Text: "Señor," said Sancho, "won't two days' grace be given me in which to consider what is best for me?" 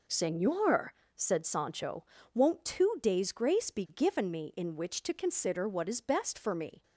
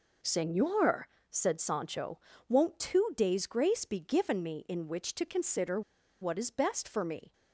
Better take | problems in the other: first | pauses between "consider" and "what"; at 5.8 s; 0.40 s long

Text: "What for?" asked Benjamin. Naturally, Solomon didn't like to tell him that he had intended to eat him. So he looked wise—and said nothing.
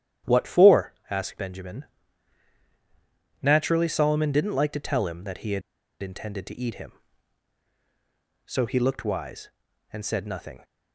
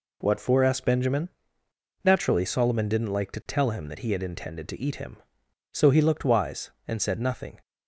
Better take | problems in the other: second | starts louder than the rest; strong; until 1.4 s; 11 dB // pauses between "had" and "intended"; at 5.6 s; 0.40 s long

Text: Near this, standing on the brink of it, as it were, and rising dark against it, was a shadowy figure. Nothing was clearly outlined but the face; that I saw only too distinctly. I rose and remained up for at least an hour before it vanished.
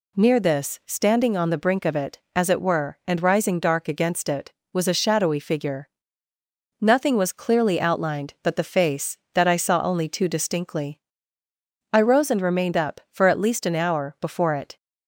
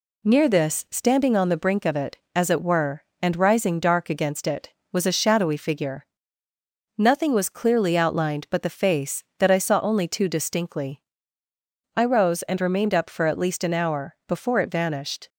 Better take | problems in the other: second | stops before "vanished"; at 14.7 s

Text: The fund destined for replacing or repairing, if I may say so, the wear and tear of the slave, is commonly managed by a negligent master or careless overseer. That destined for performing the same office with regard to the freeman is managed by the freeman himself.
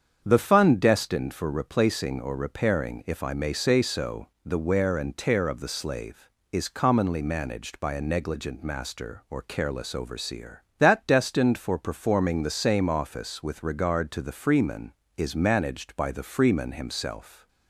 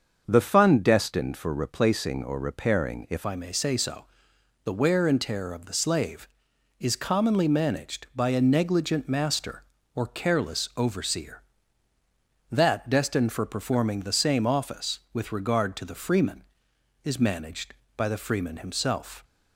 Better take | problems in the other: first | starts louder than the rest; until 1.2 s; 6.5 dB; strong in the first // changes voice at "I"; from 3.2 s on; 16.0 s long

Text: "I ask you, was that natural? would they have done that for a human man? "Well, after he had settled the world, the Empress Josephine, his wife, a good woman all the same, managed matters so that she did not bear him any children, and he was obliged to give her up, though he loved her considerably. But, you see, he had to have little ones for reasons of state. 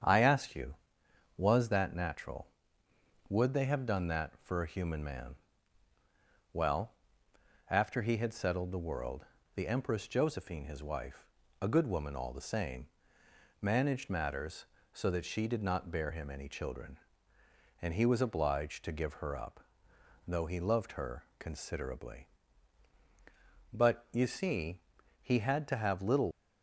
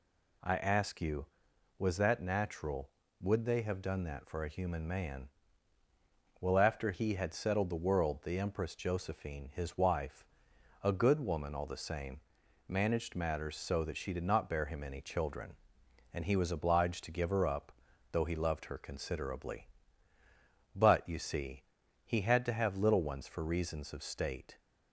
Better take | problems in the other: second | starts louder than the rest; strong; until 1.6 s; 8 dB // pauses between "her" and "considerably"; slight; at 21.2 s; 0.16 s long // stops before "ones for reasons of state"; at 26.3 s

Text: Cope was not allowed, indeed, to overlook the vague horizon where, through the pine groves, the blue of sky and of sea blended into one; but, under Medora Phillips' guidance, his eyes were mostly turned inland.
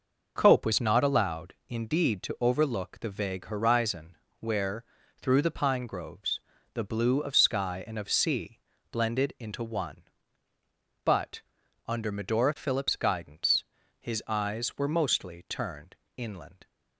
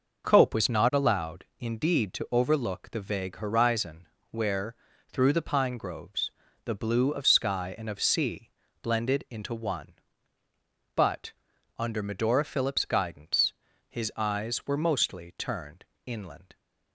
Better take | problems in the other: neither | pauses between "horizon" and "where"; slight; the same in both // pauses between "sea" and "blended"; slight; the same in both // pauses between "turned" and "inland"; slight; the same in both

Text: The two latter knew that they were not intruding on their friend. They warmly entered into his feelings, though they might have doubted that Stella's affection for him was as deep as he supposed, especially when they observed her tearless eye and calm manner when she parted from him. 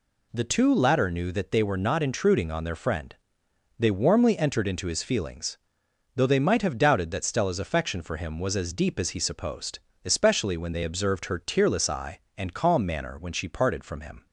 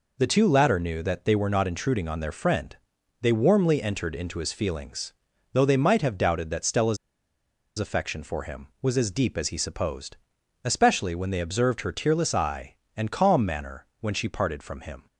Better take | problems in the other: first | pauses between "Stella's" and "affection"; noticeable; at 6.9 s; 0.81 s long // pauses between "manner" and "when"; slight; at 13.8 s; 0.16 s long

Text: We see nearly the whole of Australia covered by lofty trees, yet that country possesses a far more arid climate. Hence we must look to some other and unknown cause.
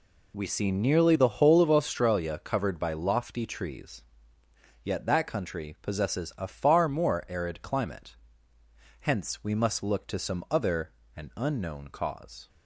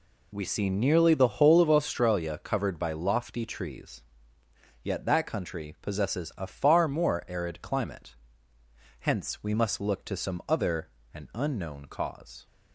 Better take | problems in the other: neither | none

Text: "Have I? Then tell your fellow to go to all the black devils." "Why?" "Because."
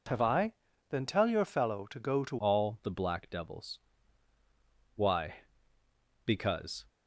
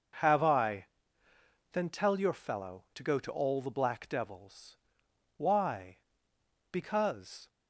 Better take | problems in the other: second | changes voice at "all"; from 2.3 s on; 4.5 s long

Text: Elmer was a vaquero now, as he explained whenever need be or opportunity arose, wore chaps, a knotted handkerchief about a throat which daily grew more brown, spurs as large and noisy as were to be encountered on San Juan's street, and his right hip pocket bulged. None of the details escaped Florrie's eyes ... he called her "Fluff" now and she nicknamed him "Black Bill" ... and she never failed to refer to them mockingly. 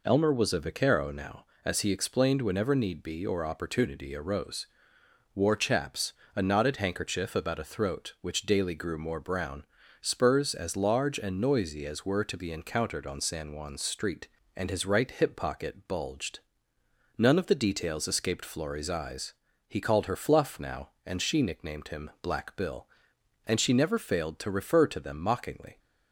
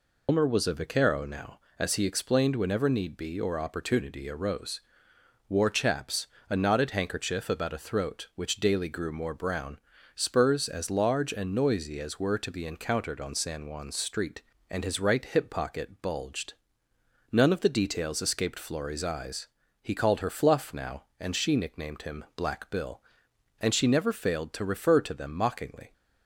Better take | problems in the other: first | loses the start of "Elmer"; at 0.2 s; 100 ms

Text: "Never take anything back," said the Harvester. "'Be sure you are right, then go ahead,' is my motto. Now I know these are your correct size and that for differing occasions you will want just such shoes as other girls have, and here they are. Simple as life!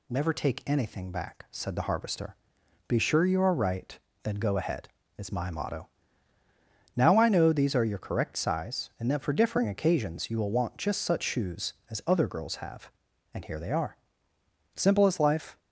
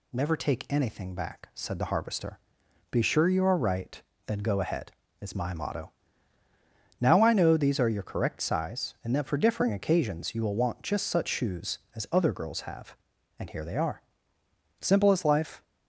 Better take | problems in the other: neither | none

